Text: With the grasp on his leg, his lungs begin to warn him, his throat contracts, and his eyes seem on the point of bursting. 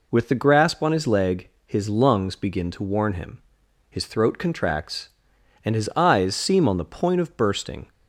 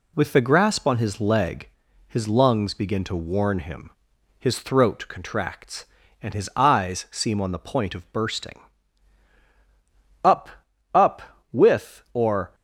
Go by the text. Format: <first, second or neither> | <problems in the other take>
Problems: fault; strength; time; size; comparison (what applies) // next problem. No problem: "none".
first | goes on to say "Up Up With or"; strong; from 10.2 s on; 2.3 s long